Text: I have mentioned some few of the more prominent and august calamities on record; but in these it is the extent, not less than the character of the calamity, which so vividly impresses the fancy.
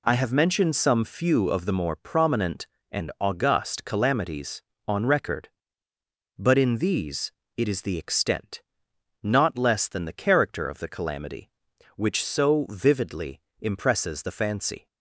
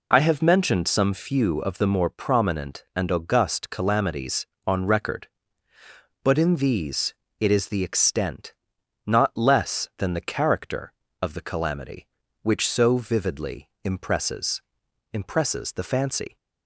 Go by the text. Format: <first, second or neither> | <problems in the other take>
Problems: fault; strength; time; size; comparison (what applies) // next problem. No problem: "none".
first | pauses between "these" and "it"; slight; at 7.1 s; 0.26 s long; slight in the first // pauses between "vividly" and "impresses"; slight; at 13.6 s; 0.16 s long; slight in the first // says "impresses" twice; at 15.1 s